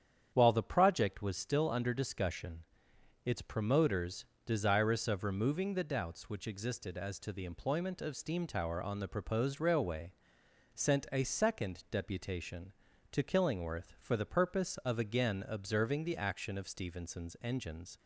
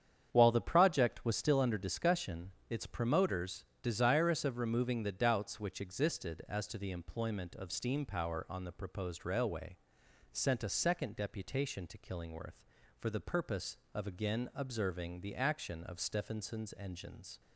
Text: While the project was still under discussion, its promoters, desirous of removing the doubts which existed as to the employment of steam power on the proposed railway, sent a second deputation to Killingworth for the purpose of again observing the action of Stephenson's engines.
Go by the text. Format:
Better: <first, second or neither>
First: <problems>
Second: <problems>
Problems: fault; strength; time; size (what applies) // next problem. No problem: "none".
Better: second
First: starts louder than the rest; strong; until 1.3 s; 8.5 dB // says "tower" for "power"; at 8.4 s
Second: starts louder than the rest; strong; until 1.3 s; 8.5 dB